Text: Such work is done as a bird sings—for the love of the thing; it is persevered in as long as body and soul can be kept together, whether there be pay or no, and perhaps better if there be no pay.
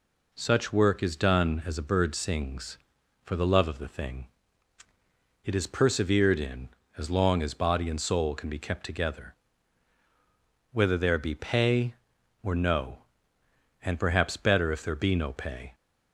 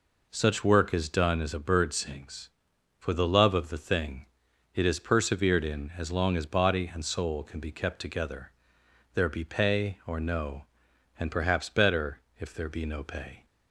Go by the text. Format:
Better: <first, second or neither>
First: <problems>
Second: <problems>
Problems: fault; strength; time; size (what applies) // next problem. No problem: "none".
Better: first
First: none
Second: skips "whether"; at 8.8 s // pauses between "better" and "if"; slight; at 12.2 s; 0.18 s long